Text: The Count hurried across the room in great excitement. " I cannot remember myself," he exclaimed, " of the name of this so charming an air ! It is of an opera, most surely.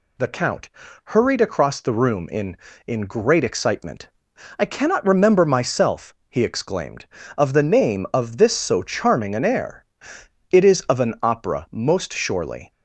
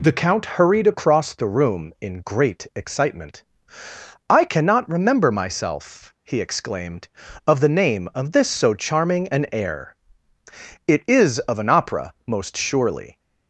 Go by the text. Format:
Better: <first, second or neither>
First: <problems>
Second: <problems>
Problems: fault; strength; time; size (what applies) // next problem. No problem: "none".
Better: second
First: pauses between "Count" and "hurried"; slight; at 0.6 s; 0.36 s long // says "in" twice; at 2.8 s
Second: none